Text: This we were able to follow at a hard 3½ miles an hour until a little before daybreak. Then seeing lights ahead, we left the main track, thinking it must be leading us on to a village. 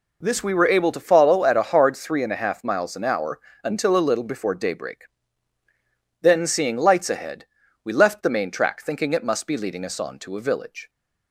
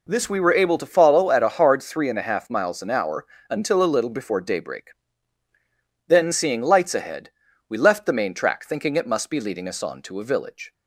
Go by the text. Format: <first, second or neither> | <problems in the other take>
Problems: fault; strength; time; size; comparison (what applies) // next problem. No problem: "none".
neither | pauses between "hour" and "until"; slight; the same in both